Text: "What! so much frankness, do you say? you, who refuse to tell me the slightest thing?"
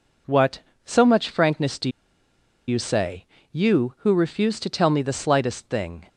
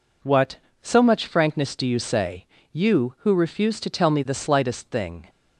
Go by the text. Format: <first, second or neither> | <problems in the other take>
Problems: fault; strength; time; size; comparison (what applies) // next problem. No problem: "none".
second | pauses between "do" and "you"; noticeable; at 1.9 s; 0.77 s long